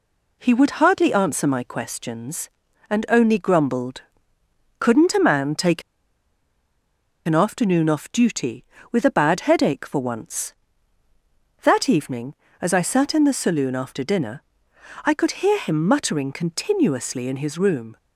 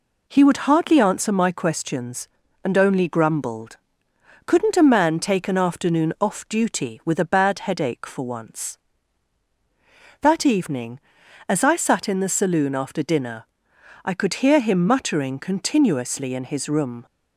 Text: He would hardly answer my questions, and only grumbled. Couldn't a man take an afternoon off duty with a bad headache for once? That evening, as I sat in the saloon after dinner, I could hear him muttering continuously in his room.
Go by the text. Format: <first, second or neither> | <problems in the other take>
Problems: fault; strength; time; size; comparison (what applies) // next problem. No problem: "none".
second | pauses between "take" and "an"; strong; at 5.8 s; 1.4 s long